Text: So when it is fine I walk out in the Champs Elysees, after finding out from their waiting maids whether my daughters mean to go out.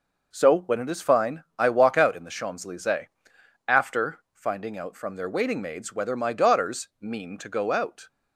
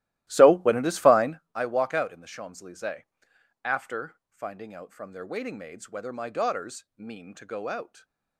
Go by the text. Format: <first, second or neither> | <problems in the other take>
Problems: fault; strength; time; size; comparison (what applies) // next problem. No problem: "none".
first | starts louder than the rest; strong; until 1.5 s; 16 dB // stays silent after the last word; slight; from 7.8 s on; 0.5 s long